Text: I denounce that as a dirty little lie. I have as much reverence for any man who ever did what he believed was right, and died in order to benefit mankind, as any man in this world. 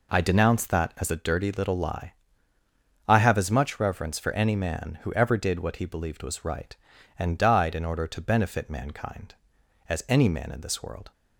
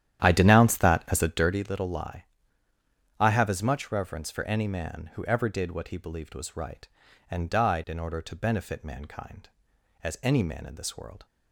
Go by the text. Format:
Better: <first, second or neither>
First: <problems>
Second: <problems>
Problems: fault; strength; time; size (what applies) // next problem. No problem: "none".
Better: first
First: none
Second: starts louder than the rest; strong; until 1.7 s; 11 dB